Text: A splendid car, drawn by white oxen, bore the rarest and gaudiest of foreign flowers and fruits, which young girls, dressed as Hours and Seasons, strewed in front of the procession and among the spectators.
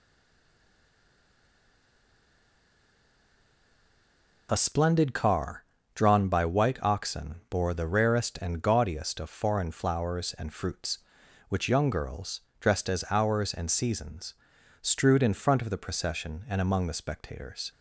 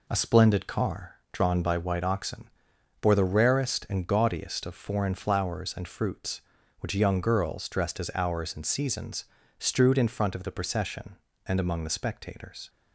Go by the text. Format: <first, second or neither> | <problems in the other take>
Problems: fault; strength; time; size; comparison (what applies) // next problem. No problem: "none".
second | stays silent before the first word; strong; until 4.4 s; 4.4 s long